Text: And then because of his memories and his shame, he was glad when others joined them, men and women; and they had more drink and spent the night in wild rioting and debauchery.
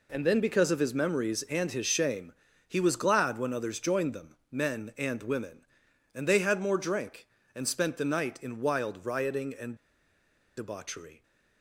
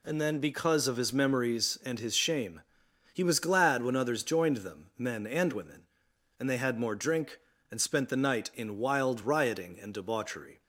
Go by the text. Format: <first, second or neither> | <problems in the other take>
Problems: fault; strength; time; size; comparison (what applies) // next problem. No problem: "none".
second | pauses between "and" and "debauchery"; noticeable; at 9.7 s; 0.80 s long